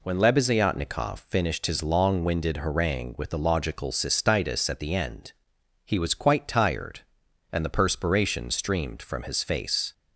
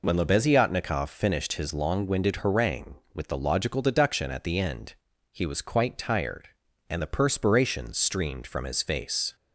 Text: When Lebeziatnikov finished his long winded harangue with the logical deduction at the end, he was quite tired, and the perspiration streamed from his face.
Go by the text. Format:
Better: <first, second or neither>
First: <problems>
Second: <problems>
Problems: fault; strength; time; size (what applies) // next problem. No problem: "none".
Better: second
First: says "cystitis" for "deduction"; at 3.9 s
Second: none